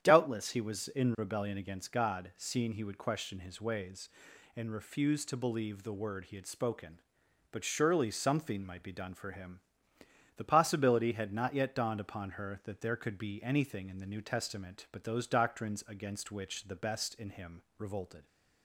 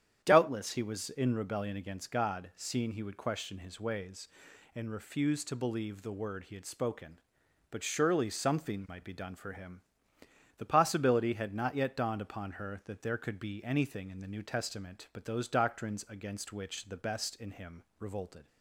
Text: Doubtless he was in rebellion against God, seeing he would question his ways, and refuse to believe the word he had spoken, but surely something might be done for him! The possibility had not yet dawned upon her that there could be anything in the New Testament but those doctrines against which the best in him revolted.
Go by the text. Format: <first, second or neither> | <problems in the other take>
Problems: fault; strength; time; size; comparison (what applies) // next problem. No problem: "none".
neither | starts louder than the rest; strong; the same in both // pauses between "him" and "revolted"; slight; the same in both